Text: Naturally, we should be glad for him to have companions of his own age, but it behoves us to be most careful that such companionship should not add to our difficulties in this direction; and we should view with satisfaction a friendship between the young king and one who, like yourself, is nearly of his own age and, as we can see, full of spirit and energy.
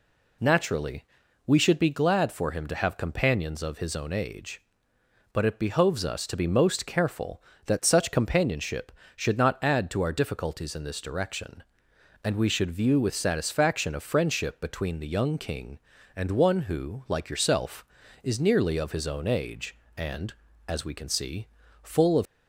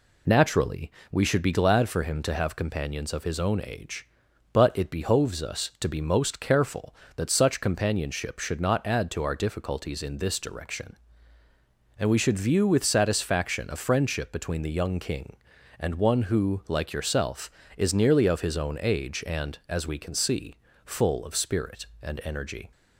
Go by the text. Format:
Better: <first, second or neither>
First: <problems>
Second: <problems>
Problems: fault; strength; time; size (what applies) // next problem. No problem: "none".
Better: second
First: stops before "spirit and energy"; at 22.2 s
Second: none